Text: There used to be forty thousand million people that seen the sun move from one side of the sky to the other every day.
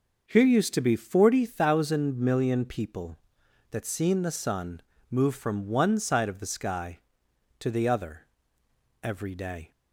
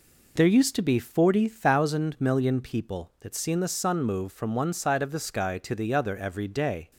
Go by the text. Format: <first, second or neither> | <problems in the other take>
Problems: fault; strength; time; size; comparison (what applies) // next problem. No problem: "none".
second | starts louder than the rest; noticeable; until 1.2 s; 6 dB // says "Here" for "There"; at 0.2 s // pauses between "sun" and "move"; slight; at 4.8 s; 0.26 s long // pauses between "other" and "every"; noticeable; at 8.2 s; 0.78 s long